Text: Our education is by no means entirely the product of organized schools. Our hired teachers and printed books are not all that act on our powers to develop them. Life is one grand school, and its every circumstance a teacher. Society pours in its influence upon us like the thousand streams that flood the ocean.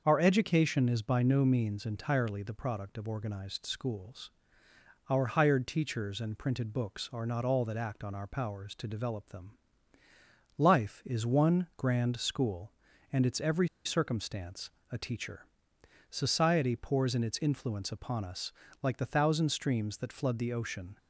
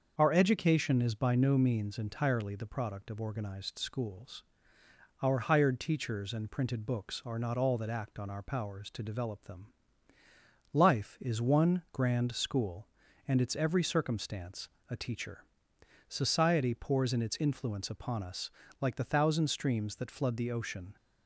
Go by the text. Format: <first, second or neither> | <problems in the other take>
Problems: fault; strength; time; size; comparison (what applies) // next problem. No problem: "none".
second | starts louder than the rest; until 1.0 s; 6.5 dB; also in the second // pauses between "every" and "circumstance"; slight; at 13.6 s; 0.17 s long // pauses between "circumstance" and "a"; slight; at 14.7 s; 0.20 s long; slight in the second // pauses between "us" and "like"; slight; at 18.5 s; 0.30 s long; slight in the second